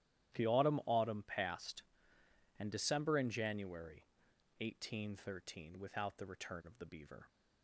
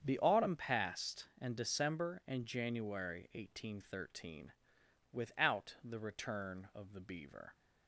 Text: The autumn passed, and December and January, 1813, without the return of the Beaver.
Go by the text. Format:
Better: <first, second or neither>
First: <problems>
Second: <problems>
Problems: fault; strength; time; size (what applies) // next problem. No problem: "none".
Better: second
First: starts louder than the rest; strong; until 1.4 s; 12.5 dB // says "autumn" twice; at 0.8 s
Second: starts louder than the rest; strong; until 1.0 s; 8 dB